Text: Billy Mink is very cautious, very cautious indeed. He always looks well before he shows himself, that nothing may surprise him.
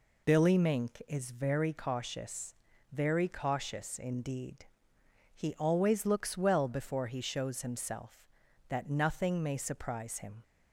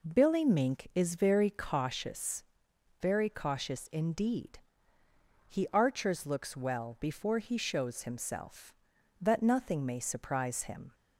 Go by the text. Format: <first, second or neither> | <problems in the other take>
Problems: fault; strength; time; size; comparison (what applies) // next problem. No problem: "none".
first | says "archers" for "always"; at 5.7 s